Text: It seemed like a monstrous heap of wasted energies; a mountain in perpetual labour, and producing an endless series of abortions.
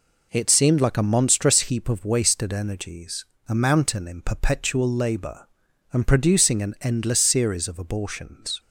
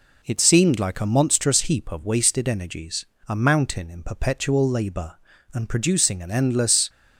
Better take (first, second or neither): first